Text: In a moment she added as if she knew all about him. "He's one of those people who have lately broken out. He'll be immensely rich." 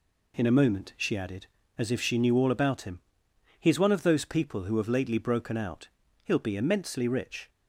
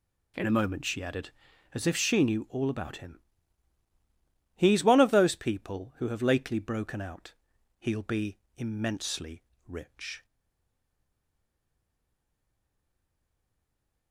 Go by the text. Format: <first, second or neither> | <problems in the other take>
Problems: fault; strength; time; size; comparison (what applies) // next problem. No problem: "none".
first | pauses between "be" and "immensely"; slight; at 8.3 s; 0.20 s long // pauses between "immensely" and "rich"; slight; at 9.4 s; 0.22 s long // stays silent after the last word; strong; from 10.2 s on; 3.9 s long